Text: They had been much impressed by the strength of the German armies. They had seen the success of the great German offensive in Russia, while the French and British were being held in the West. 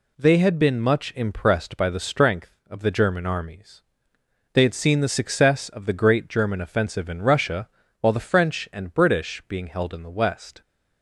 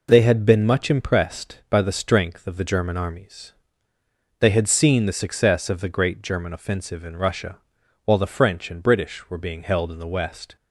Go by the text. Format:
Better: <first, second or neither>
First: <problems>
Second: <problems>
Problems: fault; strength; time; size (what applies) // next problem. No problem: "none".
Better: second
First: skips "were"; at 9.4 s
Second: none